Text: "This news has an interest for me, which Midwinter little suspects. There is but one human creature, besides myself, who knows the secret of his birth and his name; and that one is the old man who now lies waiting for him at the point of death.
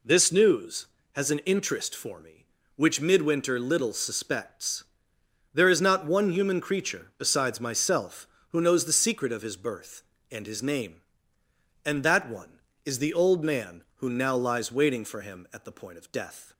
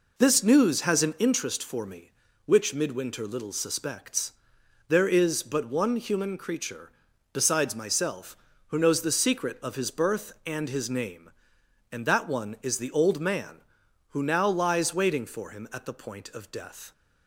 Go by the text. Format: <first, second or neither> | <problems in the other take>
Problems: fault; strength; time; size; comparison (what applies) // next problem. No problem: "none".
second | says "not" for "but"; at 5.8 s